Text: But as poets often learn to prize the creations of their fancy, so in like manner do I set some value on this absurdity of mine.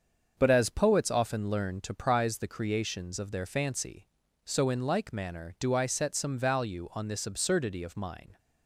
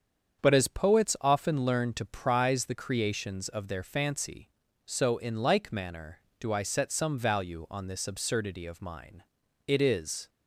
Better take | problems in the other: first | starts louder than the rest; strong; until 1.4 s; 7.5 dB; also in the first // goes on to say "It is"; noticeable; from 9.6 s on; 0.62 s long

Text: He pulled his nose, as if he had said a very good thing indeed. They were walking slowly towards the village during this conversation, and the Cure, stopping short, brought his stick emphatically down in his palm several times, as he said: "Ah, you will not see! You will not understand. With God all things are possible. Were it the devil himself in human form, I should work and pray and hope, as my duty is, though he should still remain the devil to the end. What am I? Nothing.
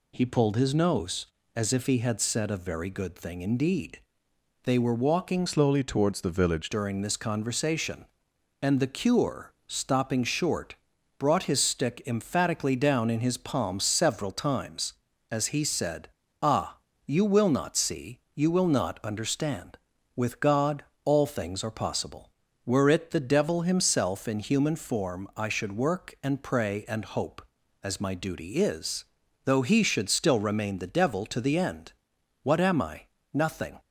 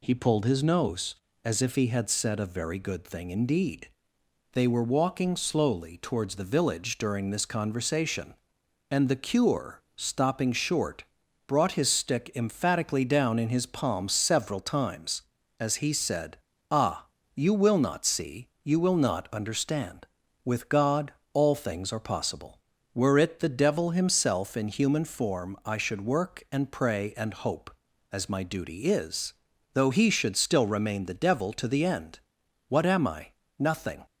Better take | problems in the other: second | changes voice from "slowly" to "village"; from 5.4 to 6.6 s; 1.2 s long // pauses between "God" and "all"; slight; at 20.8 s; 0.18 s long; slight in the second

